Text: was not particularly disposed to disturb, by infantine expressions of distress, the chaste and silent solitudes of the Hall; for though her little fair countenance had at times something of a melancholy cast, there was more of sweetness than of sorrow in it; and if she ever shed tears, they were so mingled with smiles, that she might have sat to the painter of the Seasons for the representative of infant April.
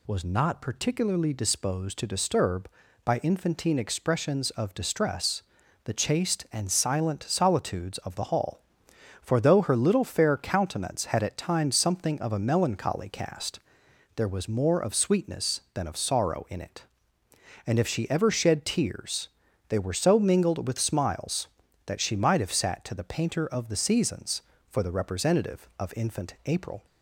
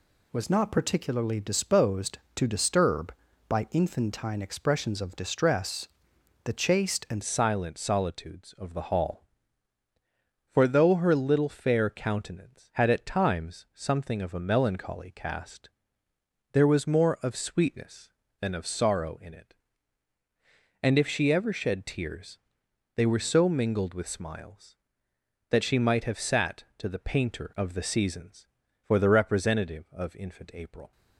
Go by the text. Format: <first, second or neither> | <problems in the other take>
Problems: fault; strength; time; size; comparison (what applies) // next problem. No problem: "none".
first | changes voice at "silent"; from 7.2 s on; 23.7 s long